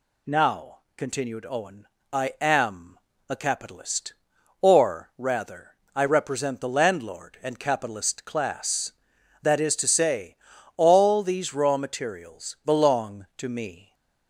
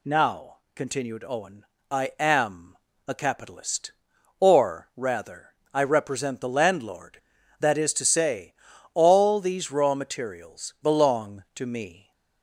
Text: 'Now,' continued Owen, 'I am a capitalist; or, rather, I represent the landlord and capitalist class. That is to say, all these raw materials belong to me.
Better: first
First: pauses between "am" and "a"; slight; at 2.9 s; 0.28 s long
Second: pauses between "am" and "a"; slight; at 2.7 s; 0.28 s long // skips "and capitalist class"; at 7.3 s

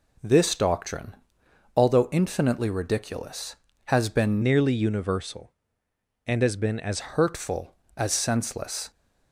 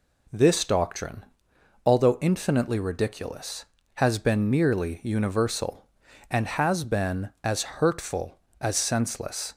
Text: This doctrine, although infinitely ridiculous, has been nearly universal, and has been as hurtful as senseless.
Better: second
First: changes voice from "nearly" to "as"; from 4.4 to 7.0 s; 2.6 s long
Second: none

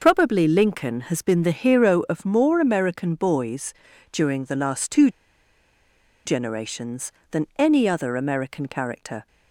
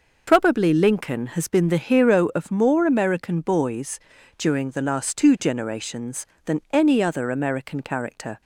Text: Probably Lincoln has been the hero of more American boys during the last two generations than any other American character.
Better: second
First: pauses between "boys" and "during"; at 3.7 s; 0.38 s long // pauses between "two" and "generations"; at 5.0 s; 1.1 s long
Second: pauses between "boys" and "during"; at 3.9 s; 0.38 s long

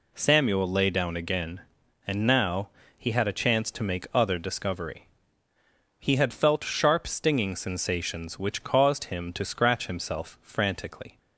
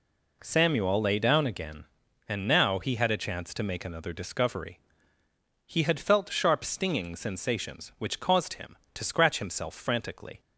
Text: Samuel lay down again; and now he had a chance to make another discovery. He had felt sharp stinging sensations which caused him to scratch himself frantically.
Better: second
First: pauses between "now" and "he"; slight; at 2.6 s; 0.26 s long // says "other" for "another"; at 4.1 s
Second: none

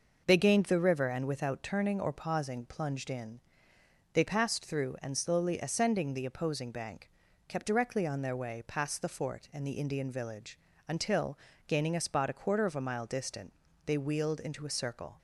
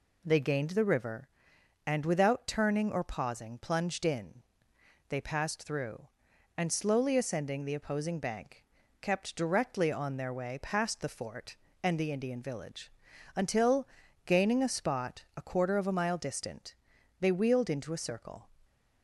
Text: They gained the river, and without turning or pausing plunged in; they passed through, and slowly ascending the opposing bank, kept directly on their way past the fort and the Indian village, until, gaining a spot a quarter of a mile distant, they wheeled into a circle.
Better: neither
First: none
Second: none

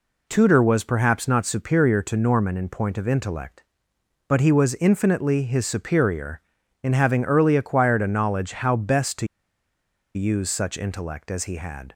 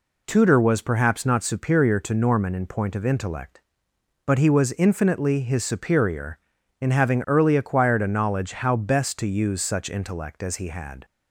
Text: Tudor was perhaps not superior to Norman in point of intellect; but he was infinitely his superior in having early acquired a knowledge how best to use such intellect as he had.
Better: second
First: pauses between "to" and "use"; noticeable; at 9.2 s; 0.88 s long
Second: none

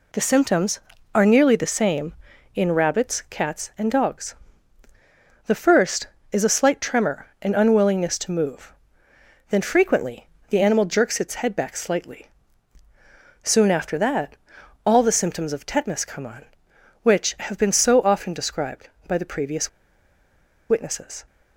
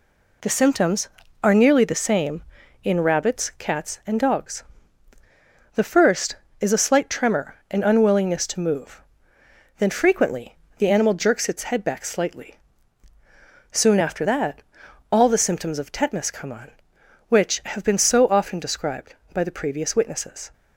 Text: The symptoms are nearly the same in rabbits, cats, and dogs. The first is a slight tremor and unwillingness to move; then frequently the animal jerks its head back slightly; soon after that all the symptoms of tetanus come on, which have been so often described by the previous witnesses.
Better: second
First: pauses between "frequently" and "the"; slight; at 10.2 s; 0.18 s long // pauses between "that" and "all"; noticeable; at 14.3 s; 0.48 s long // pauses between "previous" and "witnesses"; at 19.6 s; 1.0 s long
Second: pauses between "frequently" and "the"; slight; at 10.5 s; 0.18 s long // pauses between "that" and "all"; noticeable; at 14.6 s; 0.48 s long

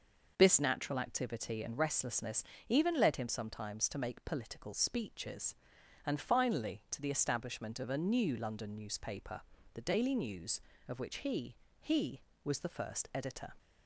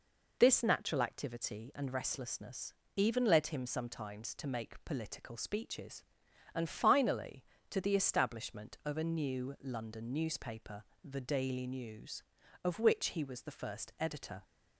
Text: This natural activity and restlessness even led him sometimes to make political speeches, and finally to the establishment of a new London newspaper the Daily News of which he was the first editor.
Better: second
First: pauses between "restlessness" and "even"; slight; at 2.4 s; 0.24 s long // pauses between "newspaper" and "the"; slight; at 9.4 s; 0.34 s long // says "he" twice; at 11.8 s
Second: pauses between "restlessness" and "even"; slight; at 2.7 s; 0.24 s long // pauses between "newspaper" and "the"; slight; at 10.8 s; 0.22 s long

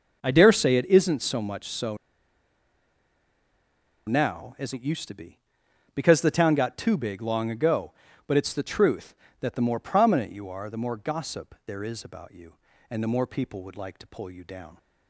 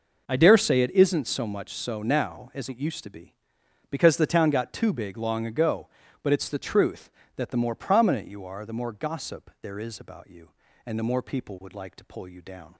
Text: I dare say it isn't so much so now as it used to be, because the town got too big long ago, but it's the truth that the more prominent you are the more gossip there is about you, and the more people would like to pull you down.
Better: second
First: pauses between "so" and "now"; strong; at 1.9 s; 2.1 s long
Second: none

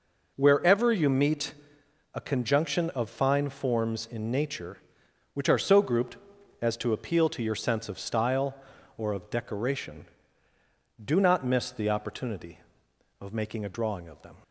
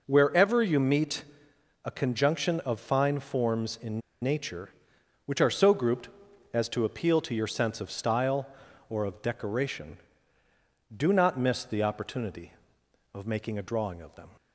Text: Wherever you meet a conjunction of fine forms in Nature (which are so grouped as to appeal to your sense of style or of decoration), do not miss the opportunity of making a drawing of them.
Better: first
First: pauses between "meet" and "a"; noticeable; at 1.5 s; 0.60 s long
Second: pauses between "meet" and "a"; noticeable; at 1.2 s; 0.60 s long // pauses between "in" and "Nature"; slight; at 4.0 s; 0.21 s long

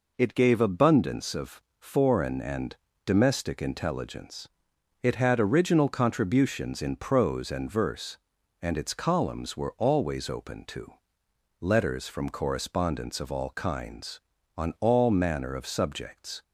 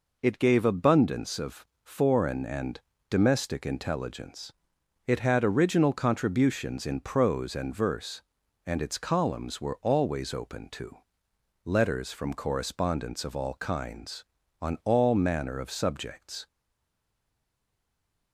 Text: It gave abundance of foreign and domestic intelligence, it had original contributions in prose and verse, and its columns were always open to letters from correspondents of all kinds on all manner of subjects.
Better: first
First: pauses between "of" and "foreign"; slight; at 1.6 s; 0.20 s long // pauses between "and" and "domestic"; slight; at 2.7 s; 0.28 s long // pauses between "to" and "letters"; noticeable; at 10.9 s; 0.70 s long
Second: pauses between "of" and "foreign"; slight; at 1.6 s; 0.20 s long // pauses between "and" and "domestic"; slight; at 2.8 s; 0.28 s long // pauses between "to" and "letters"; noticeable; at 10.9 s; 0.70 s long // stays silent after the last word; noticeable; from 16.4 s on; 1.9 s long

